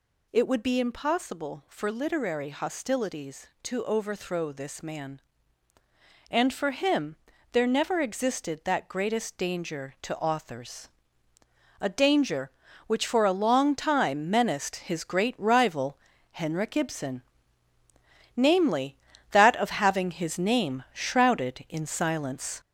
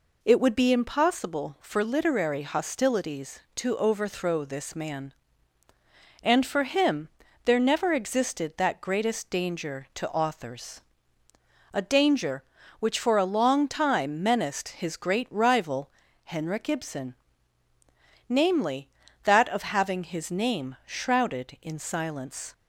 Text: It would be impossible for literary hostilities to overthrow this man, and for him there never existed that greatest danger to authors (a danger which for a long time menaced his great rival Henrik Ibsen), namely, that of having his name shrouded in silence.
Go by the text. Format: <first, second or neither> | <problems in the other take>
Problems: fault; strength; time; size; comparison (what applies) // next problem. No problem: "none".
second | gets louder; noticeable; throughout; 5 dB // pauses between "him" and "there"; slight; at 7.1 s; 0.36 s long; slight in the second // pauses between "rival" and "Henrik"; slight; at 15.9 s; 0.36 s long; slight in the second